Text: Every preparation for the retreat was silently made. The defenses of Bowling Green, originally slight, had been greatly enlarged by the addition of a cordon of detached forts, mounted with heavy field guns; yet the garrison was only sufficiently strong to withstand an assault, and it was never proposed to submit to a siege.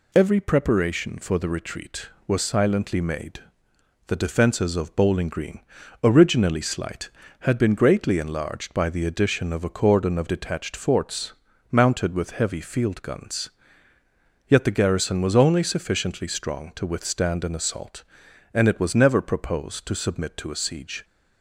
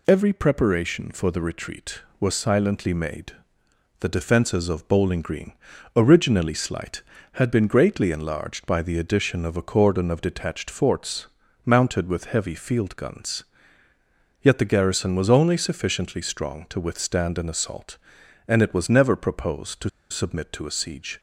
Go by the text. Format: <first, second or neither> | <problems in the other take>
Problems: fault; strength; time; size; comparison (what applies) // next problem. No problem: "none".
first | pauses between "to" and "submit"; slight; at 19.8 s; 0.21 s long